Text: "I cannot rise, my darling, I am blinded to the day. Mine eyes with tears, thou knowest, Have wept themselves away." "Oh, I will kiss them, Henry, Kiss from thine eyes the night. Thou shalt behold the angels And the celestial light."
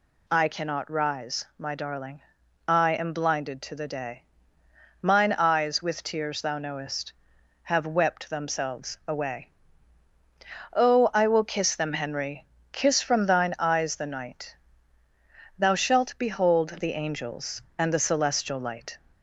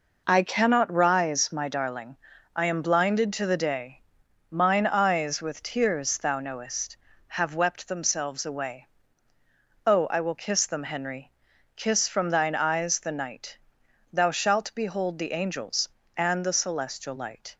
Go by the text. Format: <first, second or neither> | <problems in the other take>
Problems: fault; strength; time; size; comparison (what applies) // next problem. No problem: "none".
neither | none